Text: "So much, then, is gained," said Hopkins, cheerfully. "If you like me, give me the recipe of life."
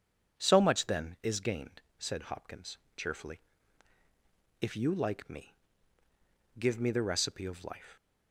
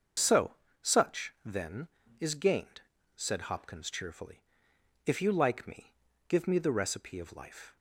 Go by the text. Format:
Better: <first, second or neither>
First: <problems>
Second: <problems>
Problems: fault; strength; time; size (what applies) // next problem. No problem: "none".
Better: first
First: none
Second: starts louder than the rest; until 1.5 s; 6.5 dB // says "such" for "much"; at 0.8 s